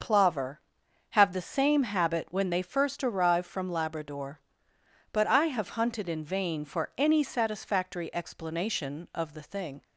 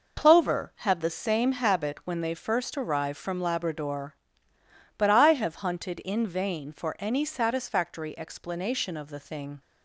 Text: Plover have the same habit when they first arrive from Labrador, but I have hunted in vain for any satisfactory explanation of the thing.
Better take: neither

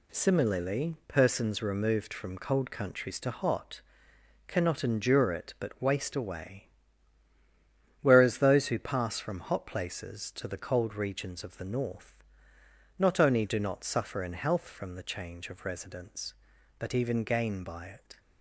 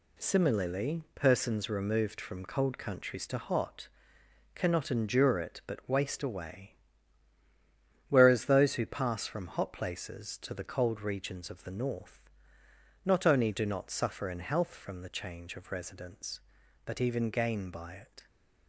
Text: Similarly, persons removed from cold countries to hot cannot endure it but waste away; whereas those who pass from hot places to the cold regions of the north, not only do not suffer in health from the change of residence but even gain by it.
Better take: neither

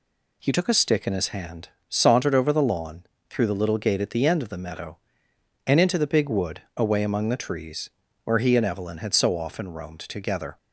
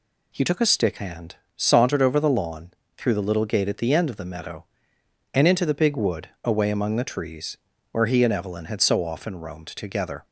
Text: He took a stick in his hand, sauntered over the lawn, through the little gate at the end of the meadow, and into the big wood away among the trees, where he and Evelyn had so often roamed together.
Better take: first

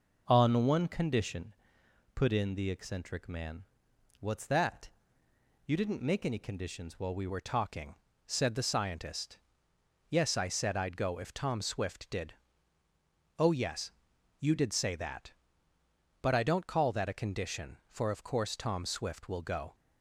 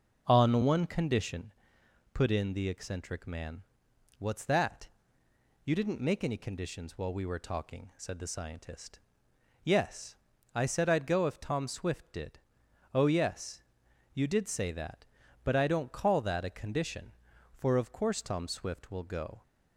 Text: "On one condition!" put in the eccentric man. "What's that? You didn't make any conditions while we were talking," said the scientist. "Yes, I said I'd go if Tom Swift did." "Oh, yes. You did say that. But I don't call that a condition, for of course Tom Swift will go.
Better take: second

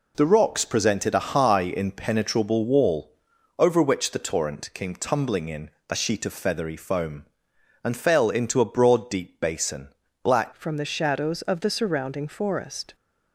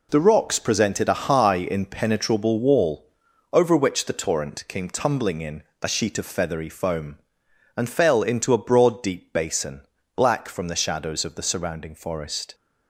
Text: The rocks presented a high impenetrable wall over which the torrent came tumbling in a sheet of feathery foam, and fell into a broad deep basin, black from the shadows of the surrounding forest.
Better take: second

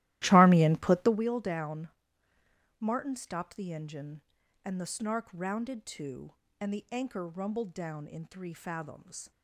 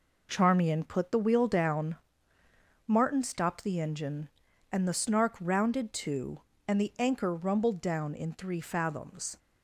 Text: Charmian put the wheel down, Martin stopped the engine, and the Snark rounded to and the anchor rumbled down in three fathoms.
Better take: second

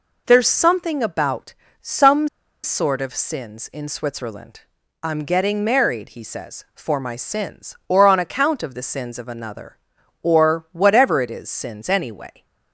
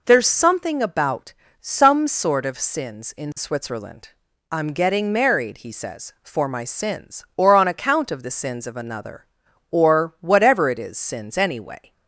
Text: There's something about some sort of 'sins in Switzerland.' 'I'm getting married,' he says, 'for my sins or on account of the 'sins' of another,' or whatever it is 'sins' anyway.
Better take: second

